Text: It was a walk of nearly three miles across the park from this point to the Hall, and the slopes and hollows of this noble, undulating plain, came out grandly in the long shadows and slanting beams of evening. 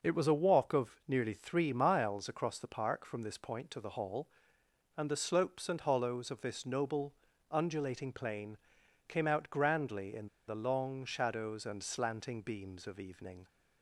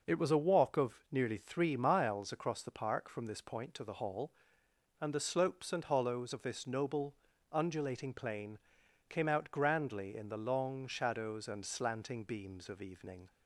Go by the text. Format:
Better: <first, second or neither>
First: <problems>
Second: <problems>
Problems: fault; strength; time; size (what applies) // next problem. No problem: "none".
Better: second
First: pauses between "in" and "the"; slight; at 10.2 s; 0.21 s long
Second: none